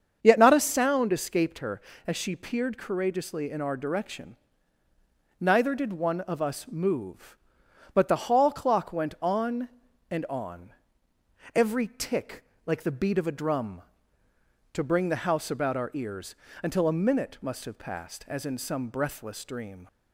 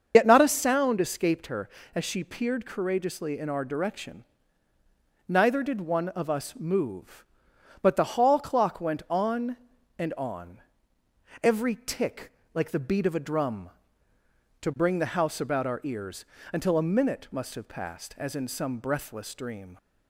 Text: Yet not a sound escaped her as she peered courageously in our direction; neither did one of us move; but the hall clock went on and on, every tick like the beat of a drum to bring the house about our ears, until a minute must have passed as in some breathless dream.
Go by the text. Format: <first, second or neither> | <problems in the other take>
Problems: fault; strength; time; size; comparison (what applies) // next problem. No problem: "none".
first | loses the start of "Yet"; at 0.1 s; 60 ms // starts louder than the rest; until 1.1 s; 7 dB; strong in the first // pauses between "tick" and "like"; slight; at 12.3 s; 0.22 s long; slight in the first